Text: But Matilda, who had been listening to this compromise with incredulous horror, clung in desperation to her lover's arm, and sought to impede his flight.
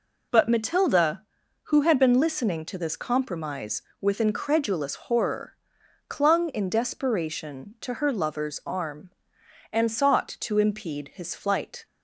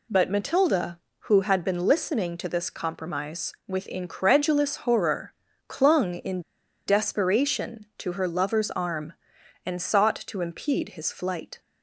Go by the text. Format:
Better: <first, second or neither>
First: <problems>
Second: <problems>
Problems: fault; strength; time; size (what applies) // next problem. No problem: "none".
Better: first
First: none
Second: pauses between "in" and "desperation"; noticeable; at 6.4 s; 0.46 s long